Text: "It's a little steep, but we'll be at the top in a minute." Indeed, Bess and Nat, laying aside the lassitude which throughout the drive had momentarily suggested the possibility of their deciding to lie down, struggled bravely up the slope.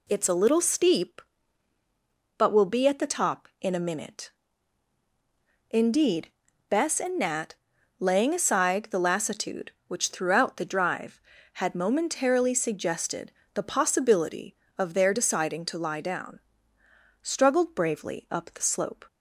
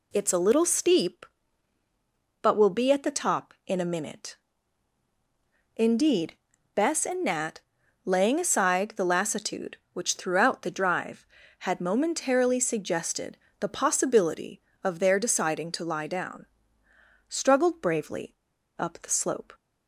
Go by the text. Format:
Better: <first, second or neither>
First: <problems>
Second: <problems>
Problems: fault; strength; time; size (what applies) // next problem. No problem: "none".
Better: first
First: pauses between "suggested" and "the"; slight; at 13.3 s; 0.24 s long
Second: pauses between "suggested" and "the"; slight; at 13.3 s; 0.24 s long // pauses between "bravely" and "up"; at 18.3 s; 0.43 s long